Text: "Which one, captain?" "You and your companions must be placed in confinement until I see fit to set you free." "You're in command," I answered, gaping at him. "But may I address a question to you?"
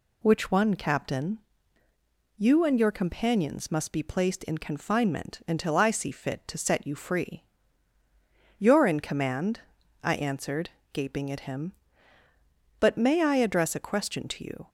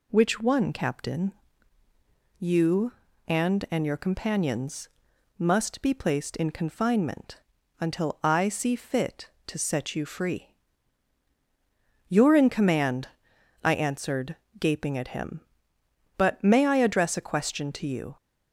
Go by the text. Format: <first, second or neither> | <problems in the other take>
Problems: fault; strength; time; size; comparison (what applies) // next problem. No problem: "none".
first | says "and" twice; at 3.7 s // pauses between "companions" and "must"; noticeable; at 4.8 s; 0.50 s long // pauses between "confinement" and "until"; at 7.4 s; 0.38 s long